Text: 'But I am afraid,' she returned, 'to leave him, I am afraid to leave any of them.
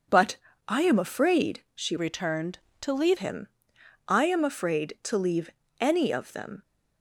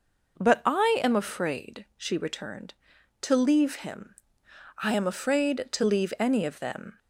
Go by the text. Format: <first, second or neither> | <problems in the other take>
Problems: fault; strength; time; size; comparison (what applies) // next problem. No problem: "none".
second | pauses between "But" and "I"; slight; at 0.3 s; 0.30 s long // changes voice from "returned" to "leave"; from 1.9 to 3.1 s; 1.2 s long // pauses between "leave" and "any"; slight; at 5.4 s; 0.32 s long